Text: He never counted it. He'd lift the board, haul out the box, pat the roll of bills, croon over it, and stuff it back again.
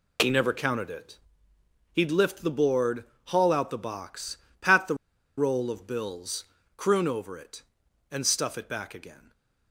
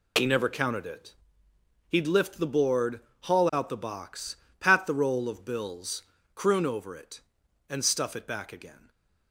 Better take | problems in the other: second | pauses between "the" and "roll"; at 4.9 s; 0.42 s long // stays silent after the last word; slight; from 9.1 s on; 0.6 s long

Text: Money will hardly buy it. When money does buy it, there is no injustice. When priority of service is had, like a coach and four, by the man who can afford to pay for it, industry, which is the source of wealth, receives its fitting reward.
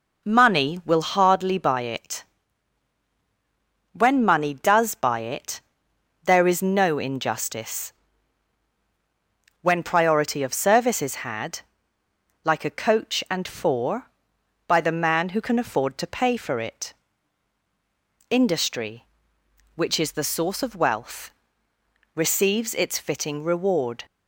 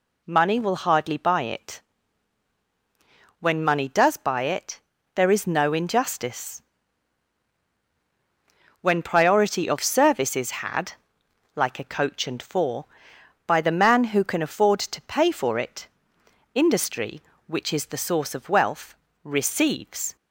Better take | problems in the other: first | stops before "its fitting reward"; at 20.1 s

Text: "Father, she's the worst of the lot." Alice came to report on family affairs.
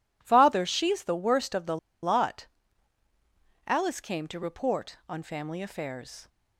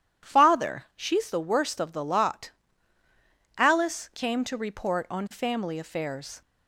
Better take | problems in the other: second | pauses between "the" and "lot"; slight; at 1.7 s; 0.26 s long

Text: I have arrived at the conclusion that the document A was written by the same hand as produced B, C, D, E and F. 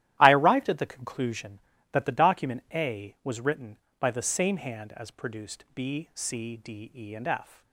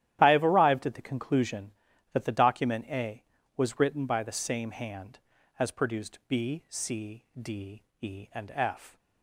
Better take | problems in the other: second | starts louder than the rest; strong; until 1.2 s; 13 dB; strong in the second // skips "have"; at 0.3 s

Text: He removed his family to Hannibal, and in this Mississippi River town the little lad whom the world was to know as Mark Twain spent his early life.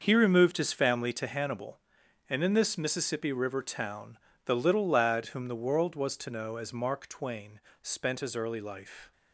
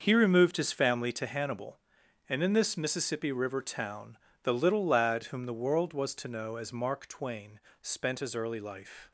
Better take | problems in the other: neither | starts louder than the rest; the same in both // pauses between "town" and "the"; slight; the same in both // pauses between "Twain" and "spent"; slight; the same in both

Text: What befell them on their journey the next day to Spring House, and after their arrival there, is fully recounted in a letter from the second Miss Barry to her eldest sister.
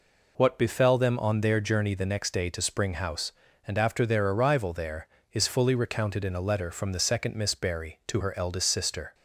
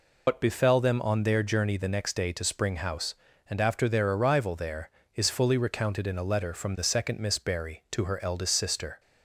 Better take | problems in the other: first | loses the start of "What"; at 0.2 s; 85 ms

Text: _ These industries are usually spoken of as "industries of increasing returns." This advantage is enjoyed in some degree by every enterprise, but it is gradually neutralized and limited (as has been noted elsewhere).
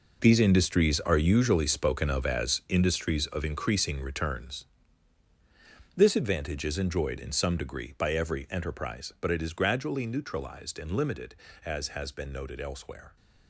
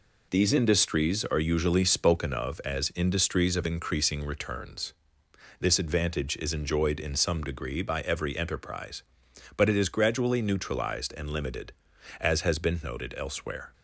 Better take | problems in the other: second | gets quieter; strong; throughout; 12.5 dB

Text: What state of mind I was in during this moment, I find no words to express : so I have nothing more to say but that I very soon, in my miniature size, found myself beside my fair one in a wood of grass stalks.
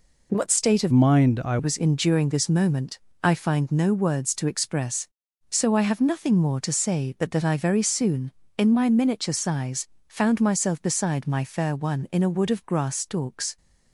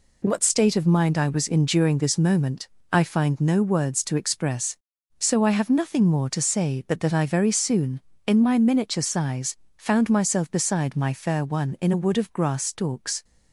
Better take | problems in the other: second | changes voice from "mind" to "I"; from 0.9 to 1.5 s; 0.6 s long

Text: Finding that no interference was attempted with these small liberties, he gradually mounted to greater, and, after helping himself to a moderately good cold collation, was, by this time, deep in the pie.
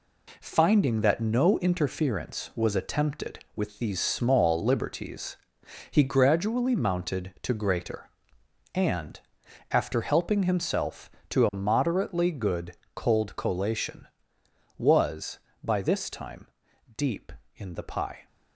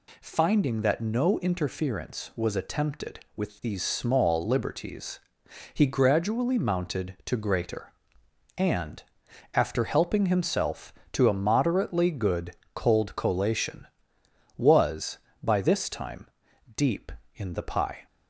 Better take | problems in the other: second | gets quieter; throughout; 6.5 dB // pauses between "good" and "cold"; slight; at 12.7 s; 0.18 s long; slight in the second

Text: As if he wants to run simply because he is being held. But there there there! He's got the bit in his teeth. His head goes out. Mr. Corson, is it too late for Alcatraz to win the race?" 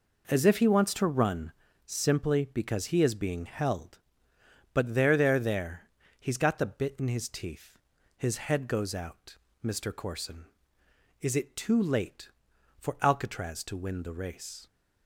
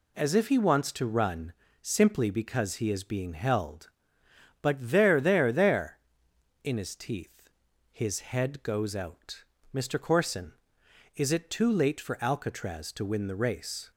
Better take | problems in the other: first | pauses between "run" and "simply"; slight; at 1.5 s; 0.30 s long; slight in the first // skips "He's got the bit"; at 6.3 s

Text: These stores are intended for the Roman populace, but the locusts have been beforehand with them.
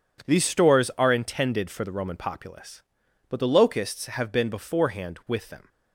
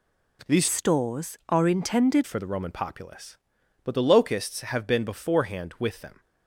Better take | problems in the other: first | changes voice from "stores" to "intended"; from 0.6 to 2.2 s; 1.6 s long

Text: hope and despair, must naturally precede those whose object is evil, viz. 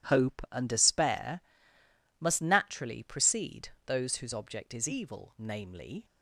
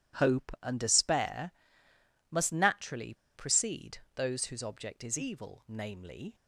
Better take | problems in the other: first | pauses between "naturally" and "precede"; slight; at 3.1 s; 0.21 s long // pauses between "precede" and "those"; slight; at 3.9 s; 0.16 s long; slight in the first

